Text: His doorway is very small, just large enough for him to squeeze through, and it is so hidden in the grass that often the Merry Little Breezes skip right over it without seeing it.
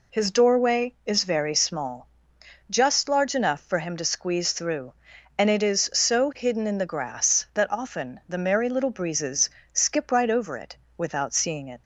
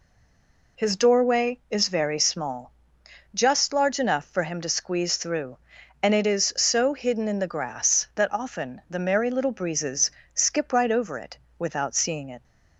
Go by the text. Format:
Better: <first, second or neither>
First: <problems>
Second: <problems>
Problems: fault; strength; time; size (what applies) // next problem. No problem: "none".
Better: first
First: pauses between "Breezes" and "skip"; slight; at 9.5 s; 0.24 s long // pauses between "it" and "without"; slight; at 10.7 s; 0.18 s long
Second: stays silent before the first word; slight; until 0.7 s; 0.7 s long // pauses between "Breezes" and "skip"; slight; at 10.1 s; 0.24 s long // pauses between "it" and "without"; slight; at 11.3 s; 0.18 s long